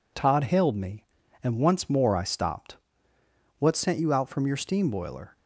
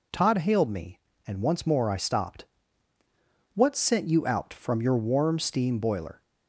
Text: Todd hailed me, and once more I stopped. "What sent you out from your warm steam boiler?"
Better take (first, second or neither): second